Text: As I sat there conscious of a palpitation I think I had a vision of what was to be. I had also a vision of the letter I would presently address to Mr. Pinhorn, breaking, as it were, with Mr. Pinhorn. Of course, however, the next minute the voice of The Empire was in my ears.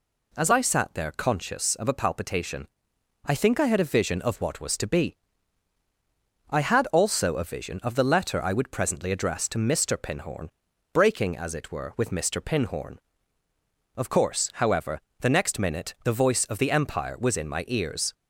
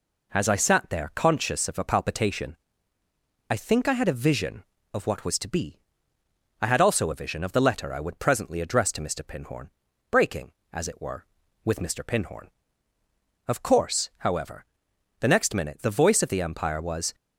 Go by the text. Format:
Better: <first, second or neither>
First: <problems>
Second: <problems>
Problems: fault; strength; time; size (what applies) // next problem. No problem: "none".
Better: first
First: pauses between "palpitation" and "I"; noticeable; at 2.6 s; 0.60 s long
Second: pauses between "palpitation" and "I"; noticeable; at 2.5 s; 0.94 s long // stops before "in my ears"; at 17.1 s